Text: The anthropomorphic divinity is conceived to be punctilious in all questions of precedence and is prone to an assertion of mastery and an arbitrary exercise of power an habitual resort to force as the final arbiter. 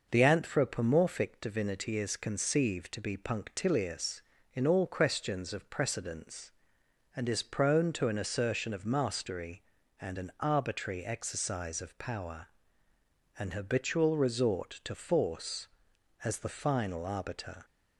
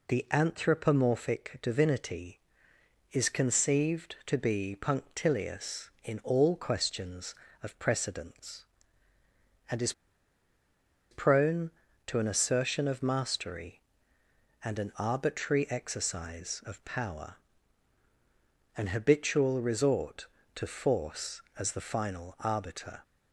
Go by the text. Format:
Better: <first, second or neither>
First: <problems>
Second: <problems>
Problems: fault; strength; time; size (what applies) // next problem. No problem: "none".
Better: first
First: pauses between "power" and "an"; noticeable; at 12.4 s; 0.90 s long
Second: pauses between "is" and "prone"; at 9.9 s; 1.1 s long // pauses between "power" and "an"; strong; at 17.3 s; 1.4 s long